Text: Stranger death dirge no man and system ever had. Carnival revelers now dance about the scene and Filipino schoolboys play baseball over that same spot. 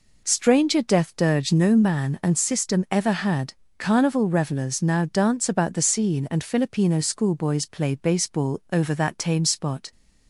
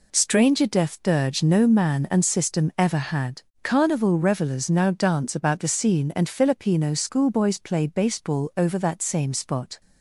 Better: second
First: says "tame" for "same"; at 9.1 s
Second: none

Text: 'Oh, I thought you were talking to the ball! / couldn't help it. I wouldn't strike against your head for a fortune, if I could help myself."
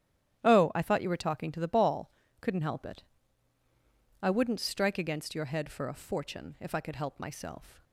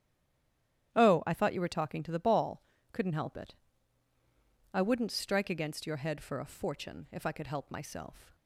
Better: first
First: starts louder than the rest; strong; until 1.4 s; 11.5 dB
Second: stays silent before the first word; slight; until 0.9 s; 0.9 s long // starts louder than the rest; strong; until 1.9 s; 11.5 dB

